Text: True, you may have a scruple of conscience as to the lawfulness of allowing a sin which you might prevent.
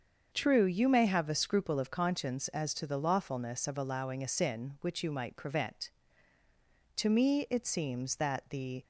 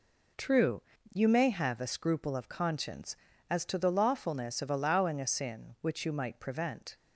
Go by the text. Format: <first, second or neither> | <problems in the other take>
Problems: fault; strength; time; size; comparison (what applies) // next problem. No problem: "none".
second | starts louder than the rest; until 1.3 s; 7 dB // goes on to say "To me it seems that the"; strong; from 6.9 s on; 1.8 s long